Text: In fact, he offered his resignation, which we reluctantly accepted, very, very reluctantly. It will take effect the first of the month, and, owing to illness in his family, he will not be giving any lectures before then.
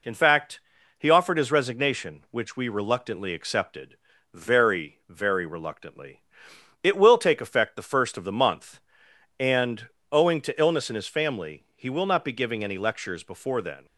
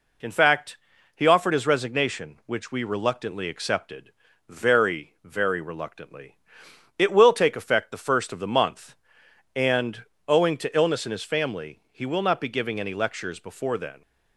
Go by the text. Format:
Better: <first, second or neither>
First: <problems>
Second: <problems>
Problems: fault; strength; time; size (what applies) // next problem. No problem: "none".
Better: neither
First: none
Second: none